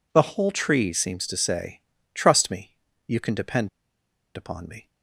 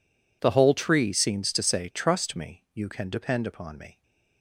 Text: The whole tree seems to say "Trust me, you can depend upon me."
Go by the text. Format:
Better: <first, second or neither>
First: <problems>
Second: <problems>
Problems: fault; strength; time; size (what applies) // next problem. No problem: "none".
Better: second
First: pauses between "say" and "Trust"; slight; at 1.8 s; 0.32 s long // pauses between "depend" and "upon"; noticeable; at 3.6 s; 0.66 s long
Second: none